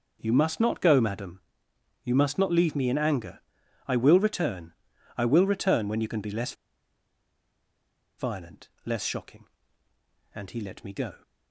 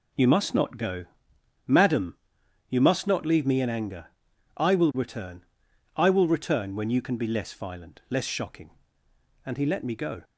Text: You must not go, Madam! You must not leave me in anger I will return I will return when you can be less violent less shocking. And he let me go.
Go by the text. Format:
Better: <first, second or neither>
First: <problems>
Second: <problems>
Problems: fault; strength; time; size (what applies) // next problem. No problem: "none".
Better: second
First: pauses between "anger" and "I"; noticeable; at 3.3 s; 0.46 s long // pauses between "return" and "I"; at 4.7 s; 0.44 s long // pauses between "less" and "violent"; strong; at 6.5 s; 1.6 s long // pauses between "violent" and "less"; slight; at 8.6 s; 0.16 s long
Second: pauses between "anger" and "I"; noticeable; at 4.0 s; 0.50 s long // pauses between "return" and "I"; noticeable; at 5.4 s; 0.50 s long